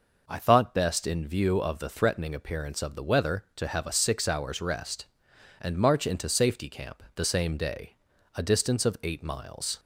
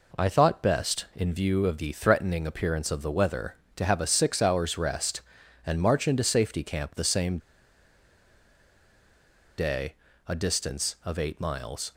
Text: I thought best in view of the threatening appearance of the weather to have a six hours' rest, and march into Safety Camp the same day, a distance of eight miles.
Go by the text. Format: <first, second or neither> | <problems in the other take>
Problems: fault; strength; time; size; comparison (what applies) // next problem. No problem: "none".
first | pauses between "same" and "day"; strong; at 7.3 s; 2.2 s long